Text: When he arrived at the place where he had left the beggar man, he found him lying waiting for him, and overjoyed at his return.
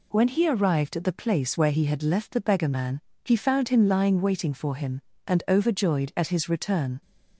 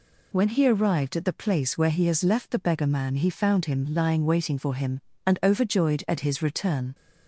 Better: first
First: none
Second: says "has" for "had"; at 2.0 s

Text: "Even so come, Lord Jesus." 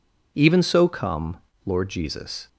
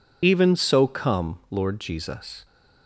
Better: first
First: none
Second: loses the start of "Even"; at 0.2 s; 30 ms

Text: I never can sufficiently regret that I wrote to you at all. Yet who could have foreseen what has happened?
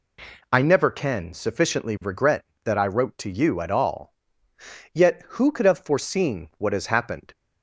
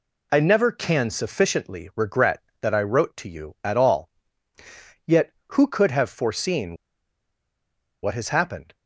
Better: first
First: none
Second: pauses between "foreseen" and "what"; strong; at 6.7 s; 1.2 s long

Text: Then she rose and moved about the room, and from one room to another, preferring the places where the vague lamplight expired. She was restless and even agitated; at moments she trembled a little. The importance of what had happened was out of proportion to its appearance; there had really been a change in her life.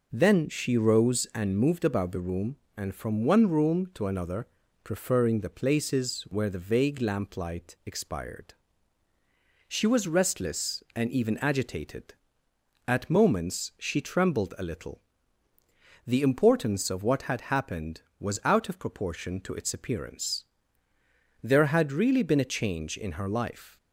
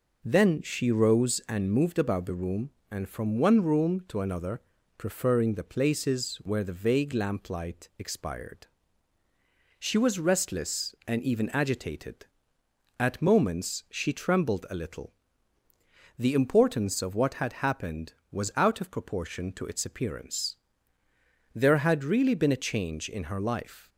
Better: neither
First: none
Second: none

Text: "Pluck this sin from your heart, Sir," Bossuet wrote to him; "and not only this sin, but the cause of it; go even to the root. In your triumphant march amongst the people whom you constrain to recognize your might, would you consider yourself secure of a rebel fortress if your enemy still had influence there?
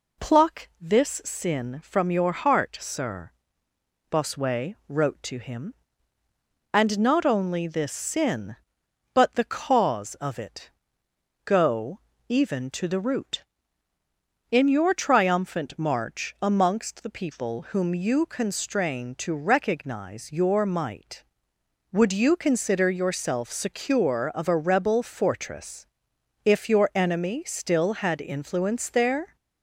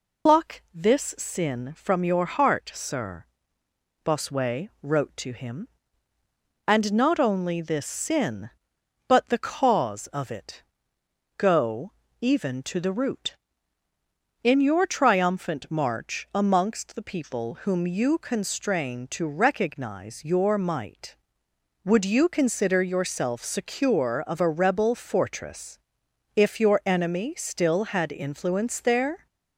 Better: first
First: pauses between "go" and "even"; slight; at 11.9 s; 0.28 s long // pauses between "fortress" and "if"; noticeable; at 25.8 s; 0.58 s long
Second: loses the start of "Pluck"; at 0.2 s; 120 ms // pauses between "go" and "even"; slight; at 11.9 s; 0.28 s long // pauses between "fortress" and "if"; noticeable; at 25.7 s; 0.56 s long

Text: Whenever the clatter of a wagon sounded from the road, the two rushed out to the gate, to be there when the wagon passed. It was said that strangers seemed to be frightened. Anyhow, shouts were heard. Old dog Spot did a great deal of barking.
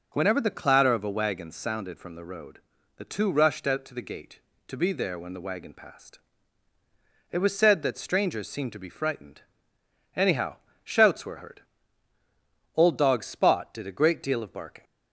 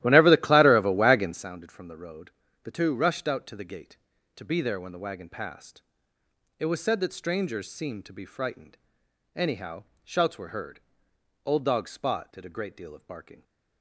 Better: first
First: none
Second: starts louder than the rest; strong; until 1.5 s; 14 dB

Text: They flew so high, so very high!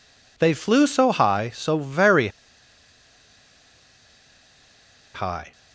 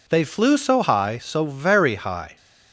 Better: second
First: pauses between "very" and "high"; strong; at 2.2 s; 2.8 s long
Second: none

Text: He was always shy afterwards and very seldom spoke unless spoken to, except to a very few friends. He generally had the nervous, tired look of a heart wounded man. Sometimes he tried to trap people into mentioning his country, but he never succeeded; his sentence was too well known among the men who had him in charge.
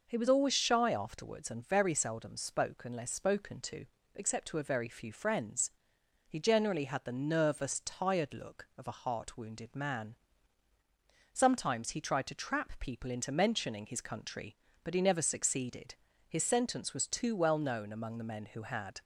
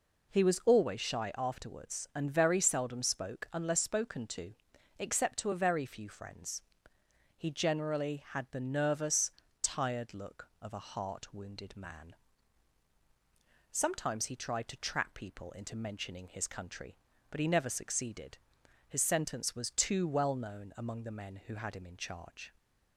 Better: second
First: stops before "him in charge"; at 19.0 s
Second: none

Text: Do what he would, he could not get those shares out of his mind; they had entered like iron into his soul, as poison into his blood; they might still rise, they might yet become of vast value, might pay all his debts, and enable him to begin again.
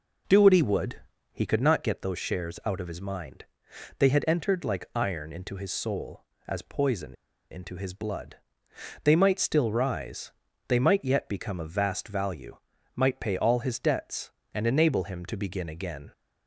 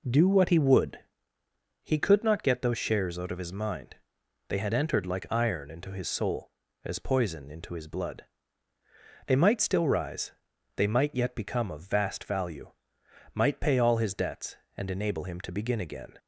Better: second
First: pauses between "poison" and "into"; slight; at 7.1 s; 0.36 s long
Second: none

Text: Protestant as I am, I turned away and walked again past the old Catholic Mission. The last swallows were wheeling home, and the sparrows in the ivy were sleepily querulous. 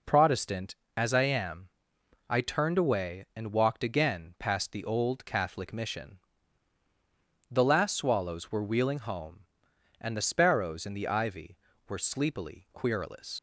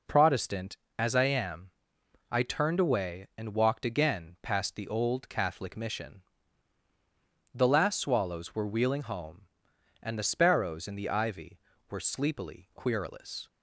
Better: second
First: leaves "querulous" unfinished; at 13.3 s; 80 ms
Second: none

